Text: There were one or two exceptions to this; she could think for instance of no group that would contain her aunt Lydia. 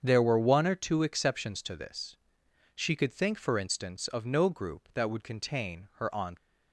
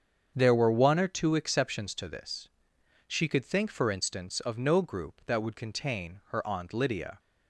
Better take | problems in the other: second | starts louder than the rest; strong; until 1.0 s; 7.5 dB; strong in the second // stops before "Lydia"; at 6.3 s

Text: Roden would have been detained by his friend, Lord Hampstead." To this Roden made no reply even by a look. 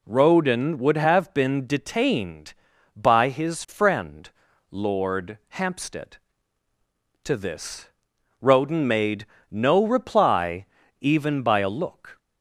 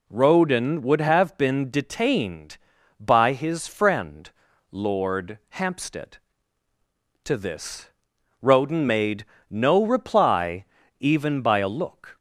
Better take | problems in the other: neither | pauses between "this" and "Roden"; noticeable; the same in both // pauses between "made" and "no"; slight; the same in both // pauses between "reply" and "even"; slight; the same in both

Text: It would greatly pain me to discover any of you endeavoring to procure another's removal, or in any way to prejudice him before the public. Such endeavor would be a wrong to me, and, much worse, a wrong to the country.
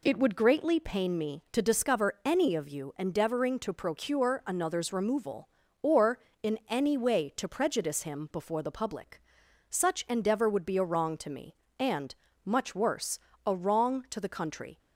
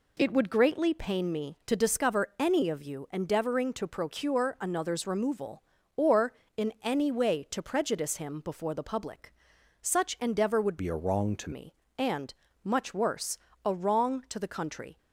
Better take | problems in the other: first | changes voice from "be" to "to"; from 10.7 to 11.5 s; 0.8 s long

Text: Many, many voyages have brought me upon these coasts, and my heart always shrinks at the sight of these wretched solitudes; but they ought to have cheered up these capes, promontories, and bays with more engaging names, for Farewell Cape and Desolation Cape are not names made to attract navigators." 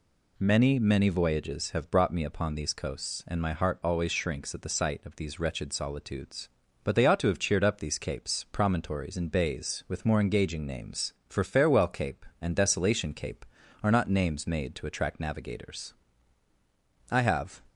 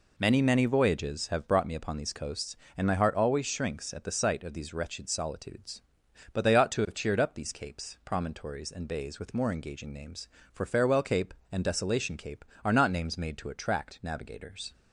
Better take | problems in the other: second | goes on to say "I have"; from 17.0 s on; 0.52 s long

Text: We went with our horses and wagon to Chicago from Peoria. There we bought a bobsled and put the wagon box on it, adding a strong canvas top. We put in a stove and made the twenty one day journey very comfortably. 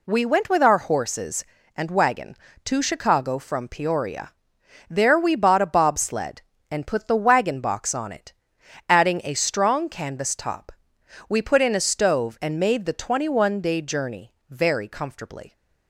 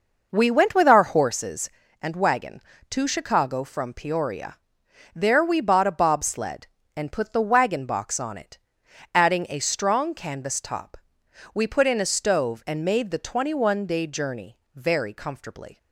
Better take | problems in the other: first | starts louder than the rest; noticeable; until 1.5 s; 5.5 dB // pauses between "journey" and "very"; slight; at 14.5 s; 0.16 s long; slight in the first

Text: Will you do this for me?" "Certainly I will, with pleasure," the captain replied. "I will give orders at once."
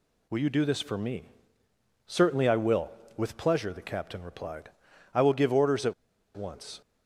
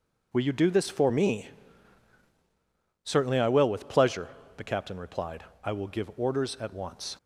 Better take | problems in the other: second | pauses between "at" and "once"; at 5.9 s; 0.43 s long

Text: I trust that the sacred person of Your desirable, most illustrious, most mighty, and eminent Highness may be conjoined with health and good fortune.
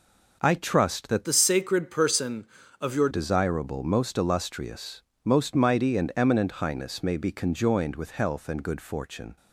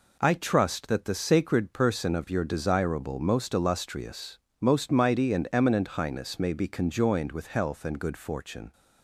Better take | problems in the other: second | changes voice from "the" to "Your"; from 1.2 to 3.0 s; 1.8 s long

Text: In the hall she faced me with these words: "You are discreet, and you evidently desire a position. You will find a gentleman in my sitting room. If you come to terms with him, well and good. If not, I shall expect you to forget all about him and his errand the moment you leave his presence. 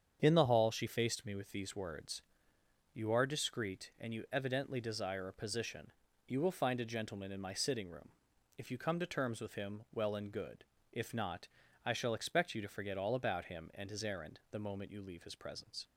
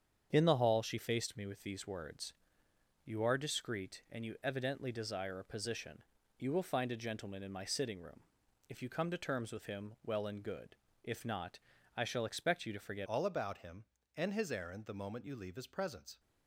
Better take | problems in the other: first | starts louder than the rest; strong; until 1.3 s; 8 dB; strong in the first // changes voice at "all"; from 13.0 s on; 3.1 s long

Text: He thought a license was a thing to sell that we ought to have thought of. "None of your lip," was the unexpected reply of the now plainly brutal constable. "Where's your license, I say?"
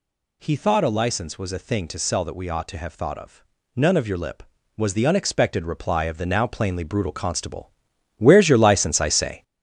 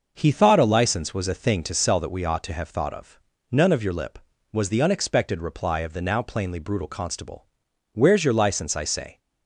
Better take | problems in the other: second | gets louder; noticeable; throughout; 5.5 dB

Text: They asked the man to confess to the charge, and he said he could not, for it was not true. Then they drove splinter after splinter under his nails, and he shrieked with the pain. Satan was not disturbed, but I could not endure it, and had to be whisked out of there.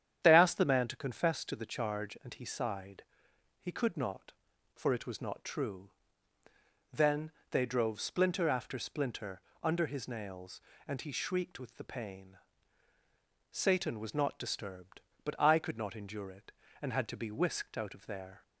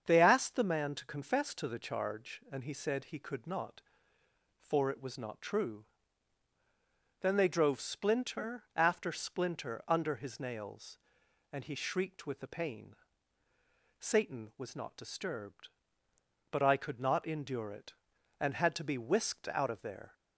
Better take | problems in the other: second | starts louder than the rest; strong; until 1.2 s; 9.5 dB; strong in the second // says "sighed" for "said"; at 2.4 s // pauses between "Then" and "they"; slight; at 7.3 s; 0.18 s long // pauses between "splinter" and "under"; slight; at 9.3 s; 0.22 s long

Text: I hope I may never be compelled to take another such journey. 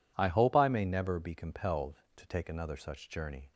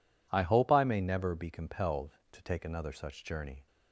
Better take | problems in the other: neither | none

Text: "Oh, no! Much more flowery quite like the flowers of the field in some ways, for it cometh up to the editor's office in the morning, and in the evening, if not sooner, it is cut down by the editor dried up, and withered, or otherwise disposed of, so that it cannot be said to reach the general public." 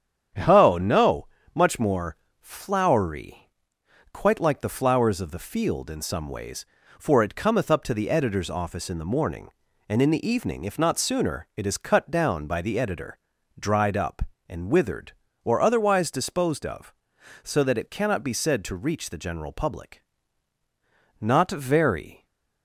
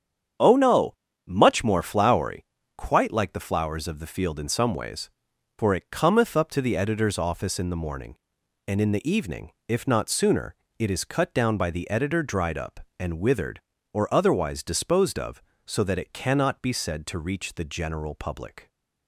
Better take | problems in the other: second | starts louder than the rest; strong; until 1.6 s; 8.5 dB; strong in the second // pauses between "more" and "flowery"; slight; at 2.1 s; 0.24 s long // pauses between "flowery" and "quite"; noticeable; at 3.3 s; 0.74 s long; slight in the second // pauses between "editor" and "dried"; at 13.1 s; 0.40 s long // goes on to say "Not very"; noticeable; from 21.1 s on; 1.0 s long

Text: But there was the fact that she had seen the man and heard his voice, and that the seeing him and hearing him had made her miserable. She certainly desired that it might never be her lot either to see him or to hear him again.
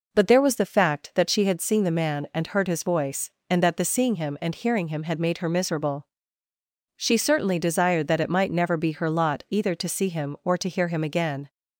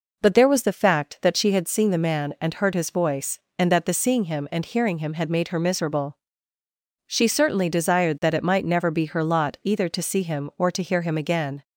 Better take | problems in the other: neither | none

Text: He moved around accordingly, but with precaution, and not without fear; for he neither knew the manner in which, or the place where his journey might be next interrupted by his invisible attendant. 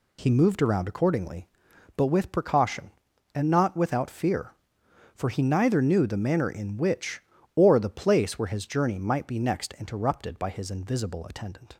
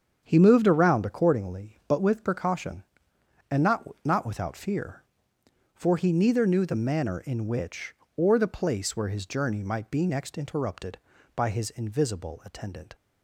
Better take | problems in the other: first | starts louder than the rest; strong; until 1.2 s; 7.5 dB // says "not" twice; at 4.0 s

